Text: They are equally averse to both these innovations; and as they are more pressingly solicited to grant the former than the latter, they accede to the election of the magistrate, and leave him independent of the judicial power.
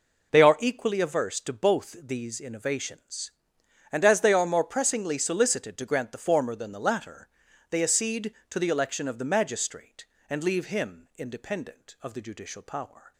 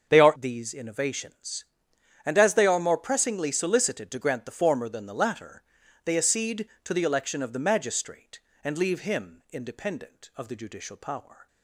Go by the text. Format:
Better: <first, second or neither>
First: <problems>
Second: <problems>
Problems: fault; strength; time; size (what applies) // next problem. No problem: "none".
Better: first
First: none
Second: starts louder than the rest; until 1.1 s; 6.5 dB // skips "equally averse to both"; at 0.3 s